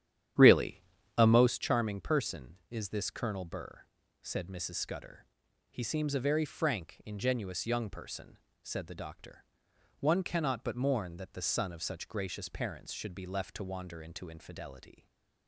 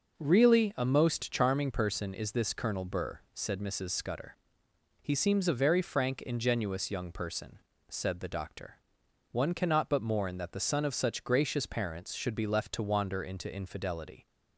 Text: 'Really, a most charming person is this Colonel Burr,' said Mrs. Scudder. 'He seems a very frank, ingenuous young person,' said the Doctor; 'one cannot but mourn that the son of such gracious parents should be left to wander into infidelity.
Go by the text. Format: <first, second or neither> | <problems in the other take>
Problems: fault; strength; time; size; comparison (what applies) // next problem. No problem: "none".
second | starts louder than the rest; strong; until 1.6 s; 10.5 dB // stays silent after the last word; slight; from 14.9 s on; 0.5 s long